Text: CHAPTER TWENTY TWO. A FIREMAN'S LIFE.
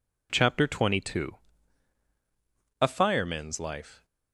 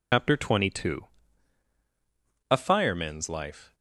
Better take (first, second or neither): first